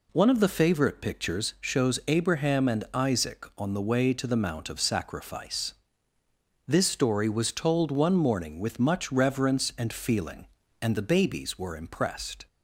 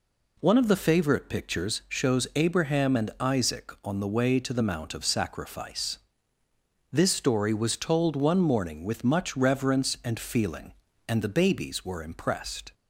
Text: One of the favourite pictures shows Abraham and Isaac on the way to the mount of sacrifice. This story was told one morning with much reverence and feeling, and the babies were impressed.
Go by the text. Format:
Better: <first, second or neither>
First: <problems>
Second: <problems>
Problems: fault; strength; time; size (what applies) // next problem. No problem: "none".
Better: neither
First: none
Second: none